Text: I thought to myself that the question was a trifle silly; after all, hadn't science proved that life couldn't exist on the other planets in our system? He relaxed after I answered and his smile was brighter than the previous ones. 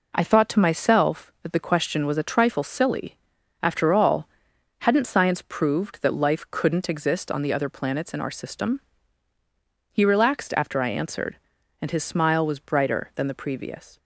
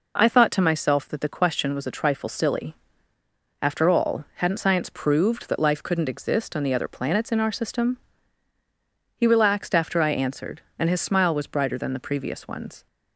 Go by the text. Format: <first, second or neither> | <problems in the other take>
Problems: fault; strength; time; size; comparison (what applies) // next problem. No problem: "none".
second | stops before "ones"; at 13.9 s